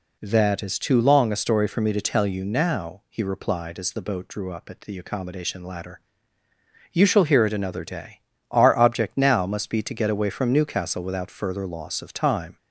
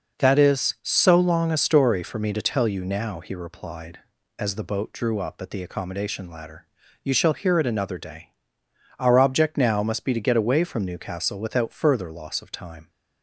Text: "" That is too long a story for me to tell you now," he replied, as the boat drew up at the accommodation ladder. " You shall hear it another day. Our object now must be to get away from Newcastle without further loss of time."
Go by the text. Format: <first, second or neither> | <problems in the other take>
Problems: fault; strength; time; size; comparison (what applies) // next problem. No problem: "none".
first | says "so" for "too"; at 0.8 s